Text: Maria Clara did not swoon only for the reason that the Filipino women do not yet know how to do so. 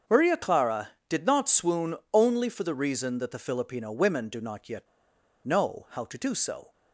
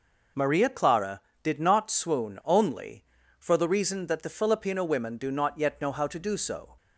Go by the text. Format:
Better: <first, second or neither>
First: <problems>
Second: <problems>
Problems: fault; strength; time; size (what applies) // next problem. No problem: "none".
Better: second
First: starts louder than the rest; until 1.2 s; 6.5 dB // pauses between "swoon" and "only"; slight; at 1.9 s; 0.18 s long // pauses between "yet" and "know"; noticeable; at 4.8 s; 0.57 s long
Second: none